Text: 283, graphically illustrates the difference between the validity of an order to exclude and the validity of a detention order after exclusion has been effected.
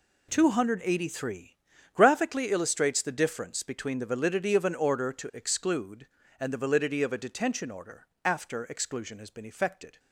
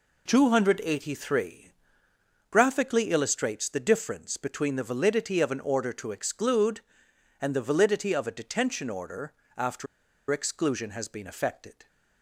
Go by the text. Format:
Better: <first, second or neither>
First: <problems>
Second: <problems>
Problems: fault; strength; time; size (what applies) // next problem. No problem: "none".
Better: first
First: pauses between "order" and "after"; slight; at 8.0 s; 0.18 s long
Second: pauses between "order" and "after"; slight; at 9.3 s; 0.26 s long // pauses between "after" and "exclusion"; at 9.8 s; 0.44 s long